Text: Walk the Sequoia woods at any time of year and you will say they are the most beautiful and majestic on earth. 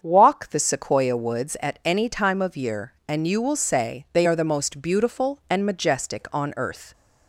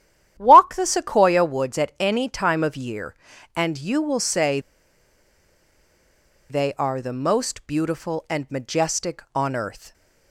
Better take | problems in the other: first | starts louder than the rest; strong; until 1.3 s; 11 dB; also in the first // pauses between "say" and "they"; strong; at 4.5 s; 1.9 s long

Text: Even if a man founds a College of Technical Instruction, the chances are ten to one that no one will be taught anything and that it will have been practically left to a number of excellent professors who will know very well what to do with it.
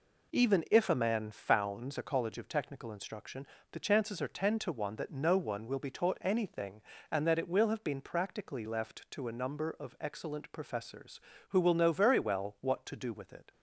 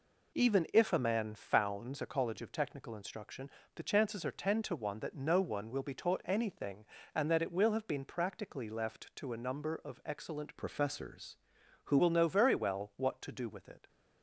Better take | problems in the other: first | changes voice from "professors" to "who"; from 10.5 to 11.9 s; 1.4 s long

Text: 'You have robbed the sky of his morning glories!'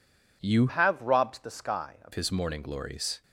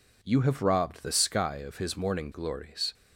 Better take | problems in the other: second | changes voice from "have" to "of"; from 0.6 to 2.1 s; 1.5 s long

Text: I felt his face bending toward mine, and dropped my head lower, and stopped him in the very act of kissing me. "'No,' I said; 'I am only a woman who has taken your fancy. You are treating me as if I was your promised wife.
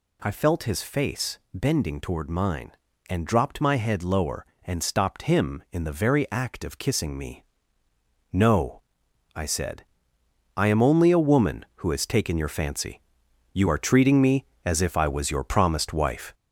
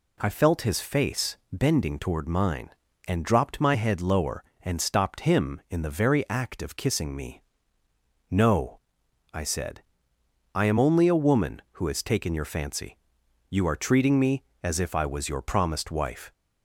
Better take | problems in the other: second | gets louder; noticeable; throughout; 4.5 dB // pauses between "face" and "bending"; slight; at 1.3 s; 0.16 s long; slight in the second

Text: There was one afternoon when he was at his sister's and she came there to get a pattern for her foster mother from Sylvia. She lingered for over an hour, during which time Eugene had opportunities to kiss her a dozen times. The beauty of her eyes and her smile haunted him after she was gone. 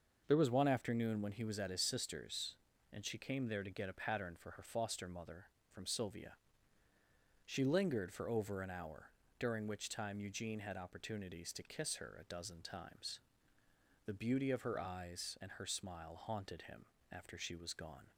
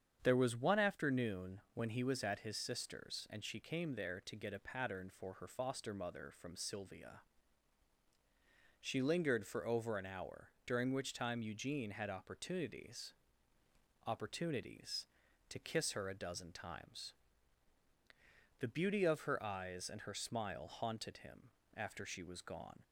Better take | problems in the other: first | starts louder than the rest; strong; until 1.2 s; 8 dB; also in the first // says "opportunities" twice; at 14.0 s // pauses between "him" and "after"; slight; at 21.5 s; 0.26 s long; slight in the first

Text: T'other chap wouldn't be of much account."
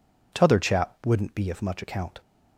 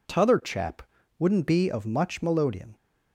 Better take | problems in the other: first | pauses between "chap" and "wouldn't"; slight; at 0.8 s; 0.34 s long // says "melodeon" for "account"; at 2.2 s

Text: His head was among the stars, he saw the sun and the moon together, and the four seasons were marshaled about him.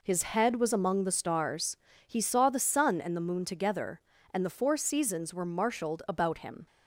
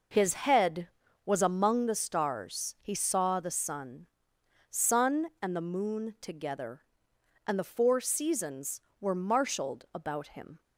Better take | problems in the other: first | says "sun" twice; at 4.6 s

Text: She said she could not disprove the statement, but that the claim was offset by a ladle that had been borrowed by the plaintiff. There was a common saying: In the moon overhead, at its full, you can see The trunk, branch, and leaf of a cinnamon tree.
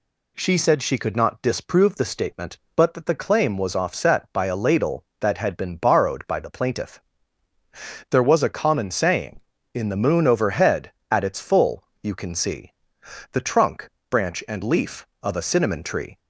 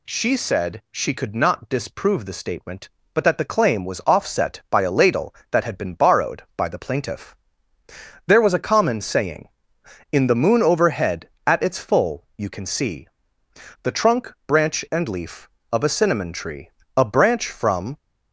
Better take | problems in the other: first | pauses between "see" and "The"; noticeable; at 13.0 s; 0.74 s long; noticeable in the first // goes on to say "A branch from"; noticeable; from 16.9 s on; 1.0 s long

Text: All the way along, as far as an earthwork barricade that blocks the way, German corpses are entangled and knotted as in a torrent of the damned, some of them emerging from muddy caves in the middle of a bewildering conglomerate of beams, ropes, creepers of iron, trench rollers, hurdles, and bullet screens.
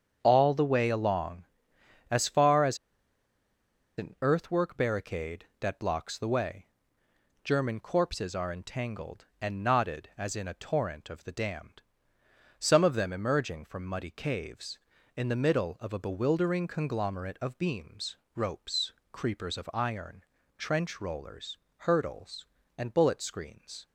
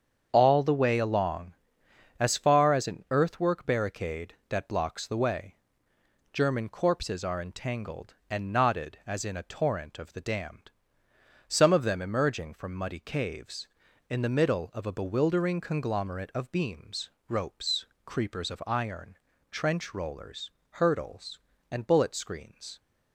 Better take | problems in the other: second | starts louder than the rest; strong; until 1.2 s; 7.5 dB; strong in the second // pauses between "as" and "an"; at 2.7 s; 1.2 s long

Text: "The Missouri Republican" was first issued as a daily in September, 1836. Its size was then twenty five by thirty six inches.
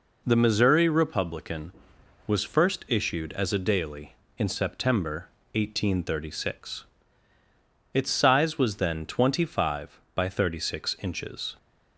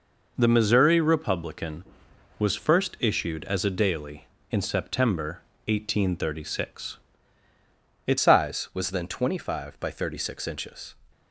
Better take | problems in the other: first | changes voice at "size"; from 8.1 s on; 2.8 s long

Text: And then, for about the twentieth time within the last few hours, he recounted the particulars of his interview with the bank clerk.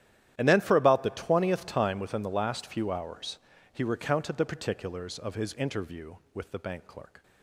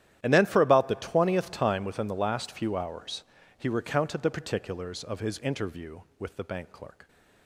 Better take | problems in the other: neither | starts louder than the rest; strong; the same in both

